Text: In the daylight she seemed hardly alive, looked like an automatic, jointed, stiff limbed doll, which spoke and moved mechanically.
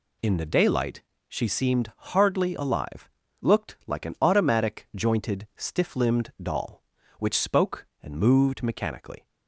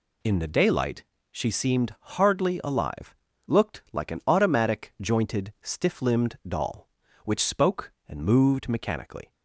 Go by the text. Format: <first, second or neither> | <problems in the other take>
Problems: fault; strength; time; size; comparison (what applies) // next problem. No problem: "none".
neither | pauses between "daylight" and "she"; slight; the same in both // pauses between "seemed" and "hardly"; slight; the same in both